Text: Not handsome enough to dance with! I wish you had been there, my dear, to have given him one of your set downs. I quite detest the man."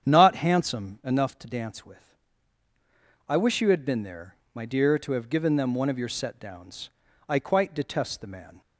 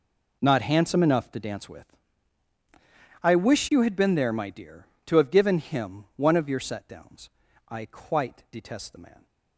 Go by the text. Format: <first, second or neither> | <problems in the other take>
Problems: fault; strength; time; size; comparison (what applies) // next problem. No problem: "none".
second | starts louder than the rest; strong; until 1.1 s; 8.5 dB // says "them" for "him"; at 5.5 s